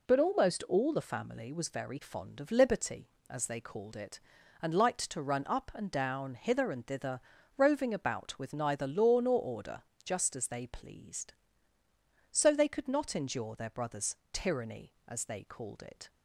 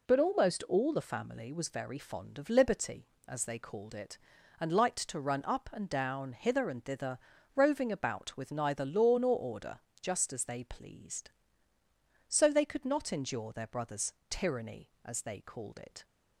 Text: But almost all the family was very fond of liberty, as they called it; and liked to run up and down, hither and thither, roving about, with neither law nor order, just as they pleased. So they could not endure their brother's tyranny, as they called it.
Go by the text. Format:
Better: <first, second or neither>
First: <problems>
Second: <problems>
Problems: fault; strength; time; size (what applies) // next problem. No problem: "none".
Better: neither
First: pauses between "brother's" and "tyranny"; slight; at 14.1 s; 0.16 s long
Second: pauses between "brother's" and "tyranny"; slight; at 14.1 s; 0.16 s long